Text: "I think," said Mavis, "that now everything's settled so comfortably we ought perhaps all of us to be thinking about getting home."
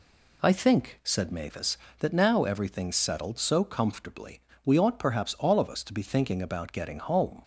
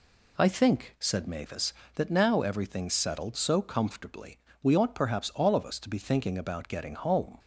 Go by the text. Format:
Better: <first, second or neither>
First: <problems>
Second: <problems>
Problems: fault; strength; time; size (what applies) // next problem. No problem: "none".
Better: neither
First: pauses between "comfortably" and "we"; slight; at 4.3 s; 0.26 s long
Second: pauses between "comfortably" and "we"; slight; at 4.3 s; 0.26 s long